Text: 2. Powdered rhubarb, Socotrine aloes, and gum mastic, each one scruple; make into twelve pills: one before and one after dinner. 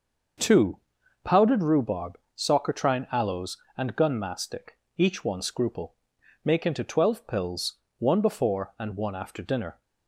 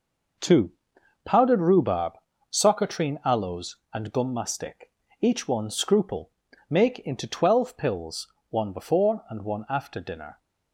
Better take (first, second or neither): second